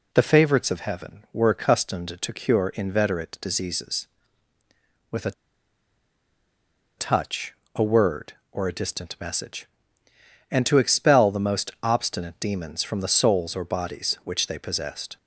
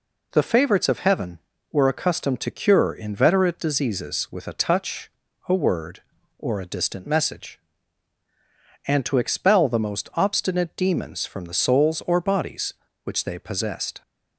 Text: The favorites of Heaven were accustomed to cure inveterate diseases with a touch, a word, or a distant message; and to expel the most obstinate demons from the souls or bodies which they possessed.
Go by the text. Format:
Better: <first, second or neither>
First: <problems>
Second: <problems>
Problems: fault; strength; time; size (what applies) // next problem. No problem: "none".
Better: second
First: pauses between "a" and "touch"; strong; at 5.3 s; 1.6 s long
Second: none